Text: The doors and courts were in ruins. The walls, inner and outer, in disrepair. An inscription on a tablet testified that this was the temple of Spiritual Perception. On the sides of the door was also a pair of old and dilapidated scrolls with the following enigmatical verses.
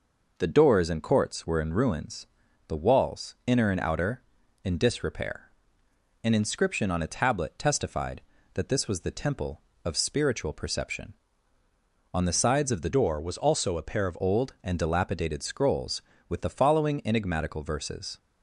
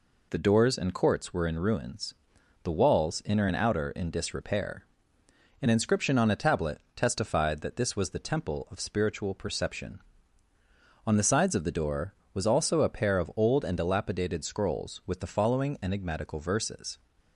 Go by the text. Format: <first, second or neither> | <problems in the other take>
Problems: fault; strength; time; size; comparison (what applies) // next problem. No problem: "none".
second | changes voice from "door" to "of"; from 12.8 to 14.1 s; 1.3 s long